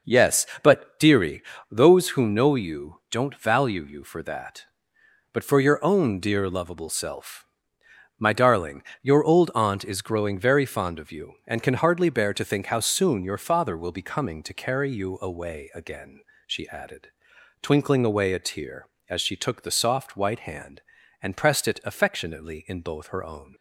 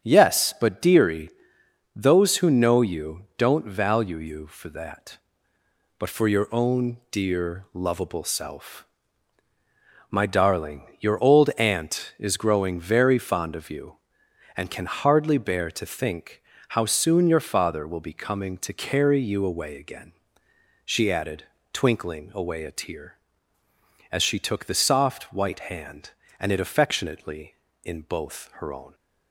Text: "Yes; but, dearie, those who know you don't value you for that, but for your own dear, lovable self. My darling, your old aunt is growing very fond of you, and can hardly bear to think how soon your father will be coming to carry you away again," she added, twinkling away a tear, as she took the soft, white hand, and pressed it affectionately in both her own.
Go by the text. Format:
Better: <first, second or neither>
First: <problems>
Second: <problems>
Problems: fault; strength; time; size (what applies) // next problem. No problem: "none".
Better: first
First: none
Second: starts louder than the rest; strong; until 1.0 s; 8 dB // pauses between "think" and "how"; slight; at 16.4 s; 0.28 s long // skips "pressed"; at 26.5 s